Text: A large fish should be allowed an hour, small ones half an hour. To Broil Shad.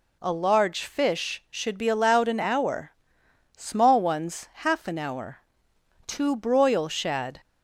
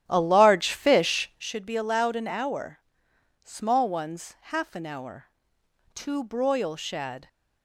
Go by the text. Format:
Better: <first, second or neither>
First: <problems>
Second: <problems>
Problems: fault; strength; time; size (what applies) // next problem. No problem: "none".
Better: first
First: none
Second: starts louder than the rest; strong; until 1.6 s; 11.5 dB